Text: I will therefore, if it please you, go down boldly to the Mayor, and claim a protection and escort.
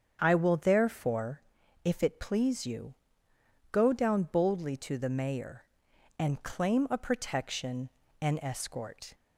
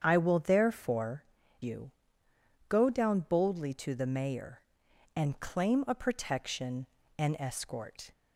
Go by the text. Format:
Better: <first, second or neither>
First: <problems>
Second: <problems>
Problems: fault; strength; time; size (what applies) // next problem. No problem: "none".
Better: first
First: starts louder than the rest; strong; until 1.2 s; 8 dB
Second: starts louder than the rest; strong; until 1.0 s; 8 dB // skips "if it please"; at 1.4 s